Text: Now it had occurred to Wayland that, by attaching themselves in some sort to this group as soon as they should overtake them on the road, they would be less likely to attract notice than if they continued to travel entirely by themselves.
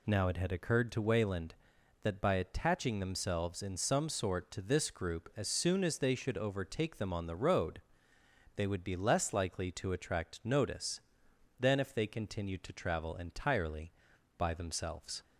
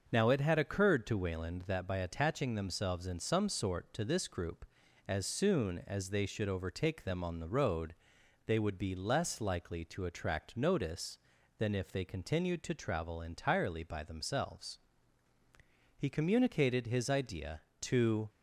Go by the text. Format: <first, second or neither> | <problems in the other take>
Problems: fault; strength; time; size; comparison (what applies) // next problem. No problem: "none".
first | starts louder than the rest; until 1.1 s; 6.5 dB // goes on to say "He communicated his idea to"; strong; from 15.9 s on; 2.3 s long